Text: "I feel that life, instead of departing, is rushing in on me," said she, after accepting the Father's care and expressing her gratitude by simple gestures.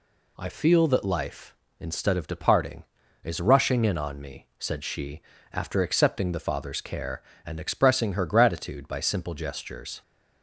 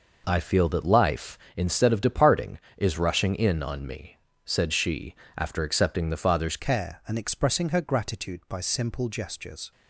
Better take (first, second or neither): first